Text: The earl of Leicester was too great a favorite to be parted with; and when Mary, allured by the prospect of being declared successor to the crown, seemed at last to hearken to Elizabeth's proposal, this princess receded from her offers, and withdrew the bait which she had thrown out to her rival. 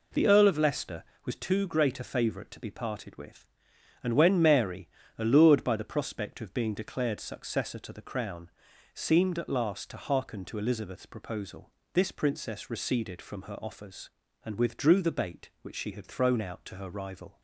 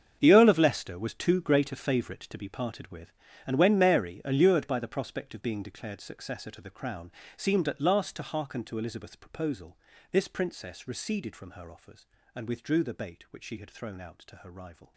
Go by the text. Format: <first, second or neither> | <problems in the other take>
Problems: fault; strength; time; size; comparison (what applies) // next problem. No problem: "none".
first | gets quieter; strong; throughout; 14.5 dB